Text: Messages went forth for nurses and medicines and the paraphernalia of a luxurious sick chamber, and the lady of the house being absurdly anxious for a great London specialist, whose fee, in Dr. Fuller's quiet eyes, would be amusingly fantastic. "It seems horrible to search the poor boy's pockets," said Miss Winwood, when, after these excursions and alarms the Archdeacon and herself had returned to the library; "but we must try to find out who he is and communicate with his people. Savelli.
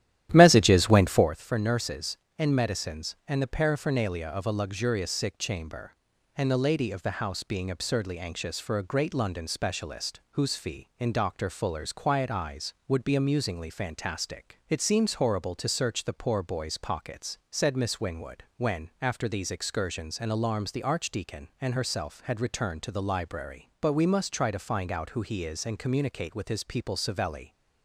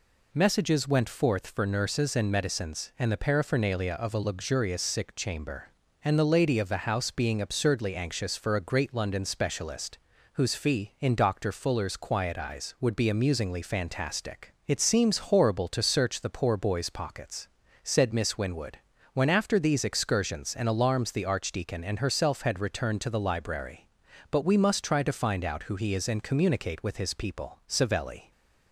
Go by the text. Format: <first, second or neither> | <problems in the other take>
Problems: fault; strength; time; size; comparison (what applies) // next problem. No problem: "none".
second | starts louder than the rest; strong; until 1.3 s; 12 dB